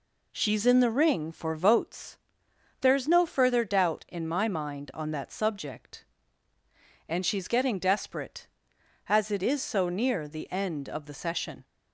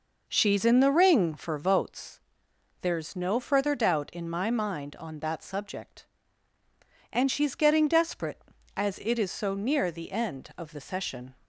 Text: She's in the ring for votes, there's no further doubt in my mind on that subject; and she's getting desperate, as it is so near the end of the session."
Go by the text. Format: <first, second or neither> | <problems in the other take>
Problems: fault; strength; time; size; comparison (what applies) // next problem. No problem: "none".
first | starts louder than the rest; noticeable; until 2.2 s; 5 dB